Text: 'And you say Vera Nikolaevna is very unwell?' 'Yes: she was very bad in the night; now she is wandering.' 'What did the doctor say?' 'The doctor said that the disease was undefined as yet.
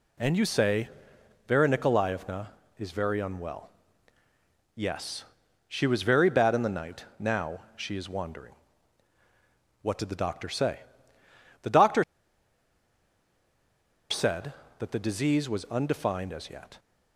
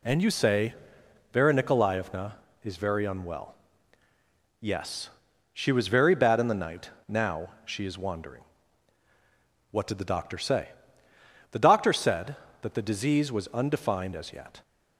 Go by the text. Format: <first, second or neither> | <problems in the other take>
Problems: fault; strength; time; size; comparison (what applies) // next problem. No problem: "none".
second | pauses between "say" and "Vera"; noticeable; at 0.8 s; 0.58 s long; noticeable in the second // pauses between "now" and "she"; slight; at 7.5 s; 0.18 s long; slight in the second // pauses between "doctor" and "said"; strong; at 12.0 s; 2.0 s long